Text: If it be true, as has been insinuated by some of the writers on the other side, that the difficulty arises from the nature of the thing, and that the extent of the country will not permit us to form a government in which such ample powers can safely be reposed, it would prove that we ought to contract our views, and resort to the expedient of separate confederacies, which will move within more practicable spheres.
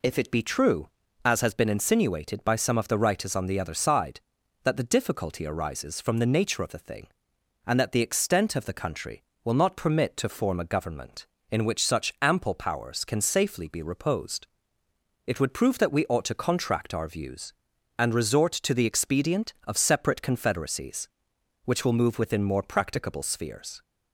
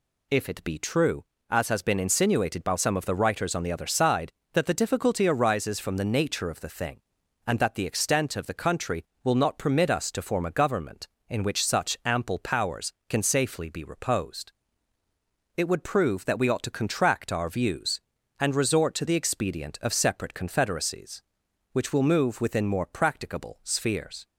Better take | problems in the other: second | skips "us"; at 10.1 s

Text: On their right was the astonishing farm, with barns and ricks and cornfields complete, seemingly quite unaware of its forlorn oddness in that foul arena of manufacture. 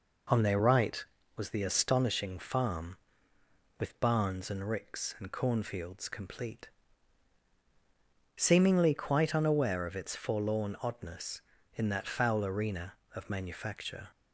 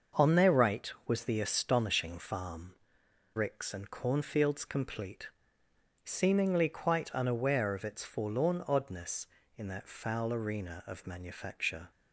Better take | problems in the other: first | starts louder than the rest; until 1.3 s; 6.5 dB // skips "with barns and"; at 3.0 s

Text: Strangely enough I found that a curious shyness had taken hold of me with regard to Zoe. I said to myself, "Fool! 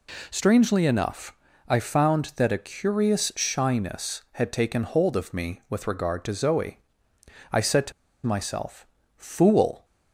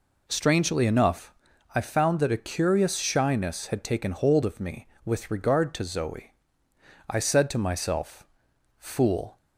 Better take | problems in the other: second | pauses between "enough" and "I"; slight; at 1.3 s; 0.32 s long; also in the second // pauses between "to" and "myself"; slight; at 7.9 s; 0.33 s long

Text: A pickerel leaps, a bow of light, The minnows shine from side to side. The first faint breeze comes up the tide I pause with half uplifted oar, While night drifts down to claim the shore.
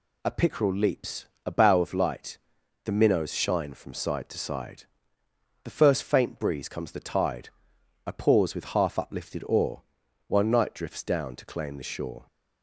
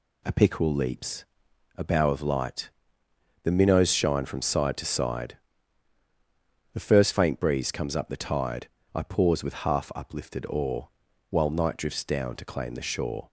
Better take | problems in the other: second | skips "up"; at 6.9 s // pauses between "tide" and "I"; noticeable; at 7.4 s; 0.56 s long; slight in the second

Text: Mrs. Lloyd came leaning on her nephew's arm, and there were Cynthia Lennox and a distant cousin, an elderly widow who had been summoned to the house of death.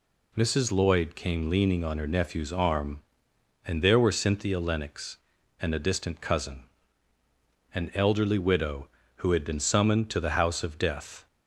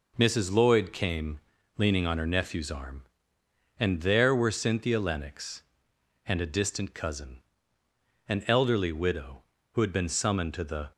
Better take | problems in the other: first | pauses between "came" and "leaning"; at 1.3 s; 0.38 s long // stops before "house of death"; at 10.9 s

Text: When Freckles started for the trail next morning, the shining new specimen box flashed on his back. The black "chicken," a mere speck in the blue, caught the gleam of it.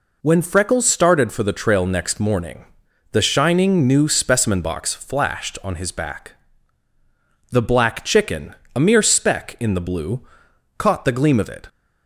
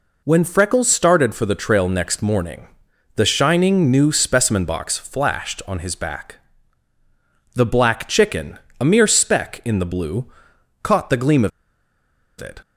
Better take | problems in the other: first | pauses between "of" and "it"; noticeable; at 11.5 s; 0.90 s long

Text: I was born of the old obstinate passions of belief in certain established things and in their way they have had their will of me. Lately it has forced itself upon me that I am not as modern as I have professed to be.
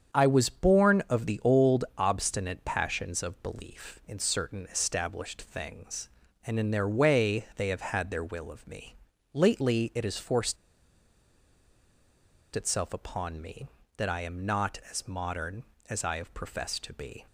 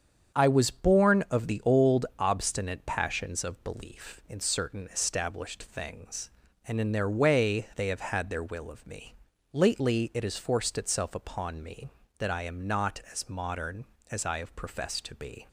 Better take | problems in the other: second | starts louder than the rest; strong; until 1.1 s; 8 dB; strong in the second // pauses between "forced" and "itself"; strong; at 10.5 s; 1.9 s long

